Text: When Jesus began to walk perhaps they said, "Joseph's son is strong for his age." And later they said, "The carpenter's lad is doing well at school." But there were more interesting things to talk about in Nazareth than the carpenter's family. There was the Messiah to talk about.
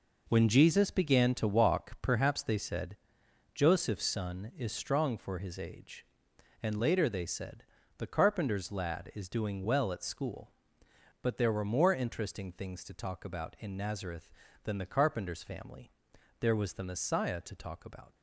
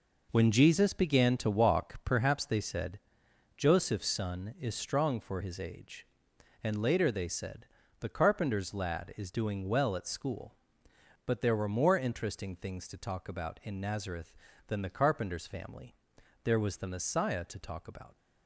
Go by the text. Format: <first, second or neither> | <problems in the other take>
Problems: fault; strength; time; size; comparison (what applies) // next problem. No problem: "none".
neither | none